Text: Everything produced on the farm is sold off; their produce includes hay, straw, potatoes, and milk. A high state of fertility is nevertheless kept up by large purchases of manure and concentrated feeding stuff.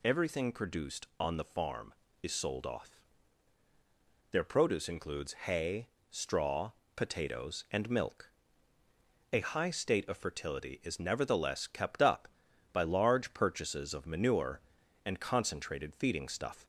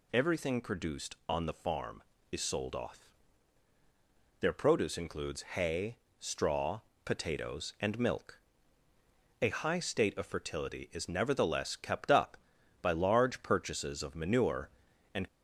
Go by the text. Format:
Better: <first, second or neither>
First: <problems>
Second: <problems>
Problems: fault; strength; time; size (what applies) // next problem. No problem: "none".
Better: first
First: none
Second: stops before "concentrated feeding stuff"; at 15.2 s